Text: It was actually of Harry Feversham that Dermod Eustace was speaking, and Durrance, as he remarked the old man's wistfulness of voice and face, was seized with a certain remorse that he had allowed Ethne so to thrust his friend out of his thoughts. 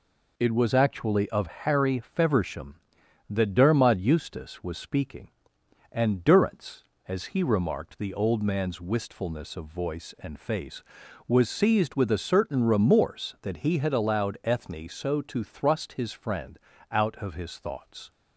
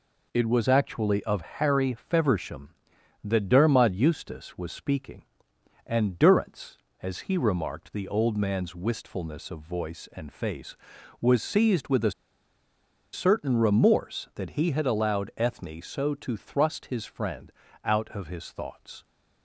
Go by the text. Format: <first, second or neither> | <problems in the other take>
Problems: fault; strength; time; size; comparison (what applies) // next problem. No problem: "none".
first | pauses between "a" and "certain"; at 12.1 s; 1.0 s long // pauses between "friend" and "out"; slight; at 17.5 s; 0.32 s long; slight in the first